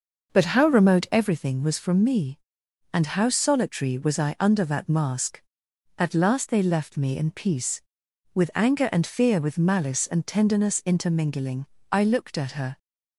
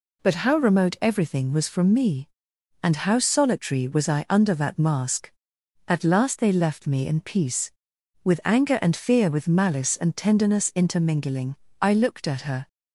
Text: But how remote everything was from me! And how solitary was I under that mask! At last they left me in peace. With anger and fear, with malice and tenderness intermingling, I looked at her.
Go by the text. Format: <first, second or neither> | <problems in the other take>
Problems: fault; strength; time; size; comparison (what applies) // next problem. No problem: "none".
second | starts louder than the rest; noticeable; until 1.3 s; 6 dB